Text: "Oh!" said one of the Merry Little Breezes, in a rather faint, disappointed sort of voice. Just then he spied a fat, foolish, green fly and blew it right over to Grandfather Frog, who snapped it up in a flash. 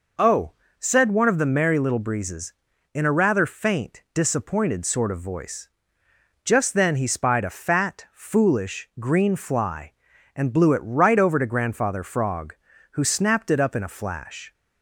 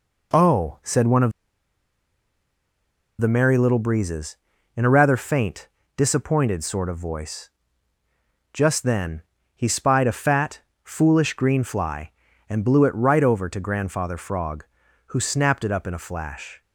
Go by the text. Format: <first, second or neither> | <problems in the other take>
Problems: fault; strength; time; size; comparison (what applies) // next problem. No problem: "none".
first | pauses between "of" and "the"; strong; at 1.3 s; 1.8 s long // pauses between "then" and "he"; slight; at 9.2 s; 0.34 s long